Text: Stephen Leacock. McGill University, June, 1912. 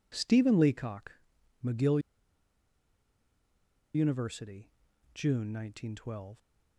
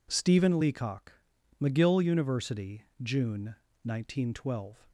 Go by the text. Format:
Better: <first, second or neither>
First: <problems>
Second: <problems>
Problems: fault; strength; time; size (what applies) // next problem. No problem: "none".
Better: second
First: pauses between "McGill" and "University"; strong; at 1.9 s; 1.9 s long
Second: none